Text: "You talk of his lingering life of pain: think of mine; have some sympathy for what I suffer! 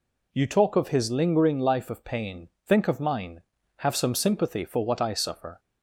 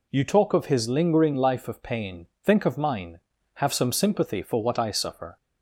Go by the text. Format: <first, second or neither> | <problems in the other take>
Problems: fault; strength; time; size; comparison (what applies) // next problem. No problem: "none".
neither | none